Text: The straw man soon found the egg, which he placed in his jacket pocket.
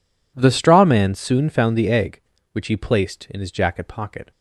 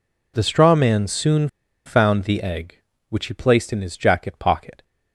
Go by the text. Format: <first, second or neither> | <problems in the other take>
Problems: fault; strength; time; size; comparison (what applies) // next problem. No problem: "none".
first | pauses between "soon" and "found"; at 1.4 s; 0.39 s long